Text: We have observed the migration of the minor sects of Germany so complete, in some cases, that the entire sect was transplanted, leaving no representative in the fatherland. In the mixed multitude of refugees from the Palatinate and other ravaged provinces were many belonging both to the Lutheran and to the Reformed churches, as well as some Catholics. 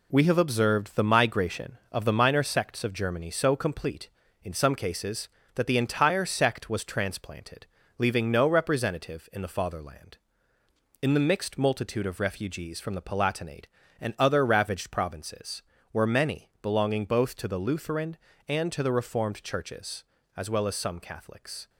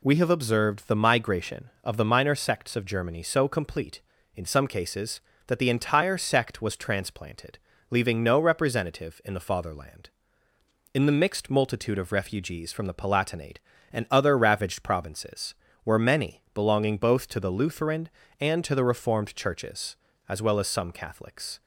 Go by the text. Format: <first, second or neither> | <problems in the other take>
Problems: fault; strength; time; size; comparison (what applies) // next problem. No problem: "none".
second | gets quieter; noticeable; throughout; 5.5 dB